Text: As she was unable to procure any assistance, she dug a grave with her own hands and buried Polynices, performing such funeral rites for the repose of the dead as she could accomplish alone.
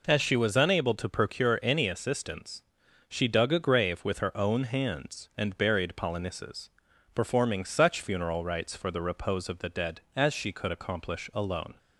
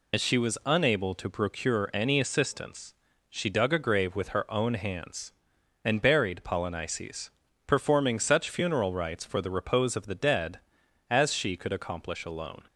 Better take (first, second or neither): first